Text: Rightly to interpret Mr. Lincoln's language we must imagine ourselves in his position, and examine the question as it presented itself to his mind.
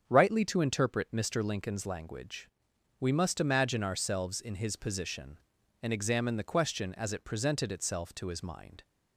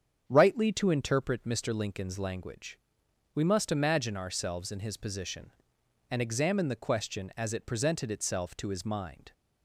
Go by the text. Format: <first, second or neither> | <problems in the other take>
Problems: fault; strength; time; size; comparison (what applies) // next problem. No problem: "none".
neither | starts louder than the rest; strong; the same in both // pauses between "language" and "we"; noticeable; the same in both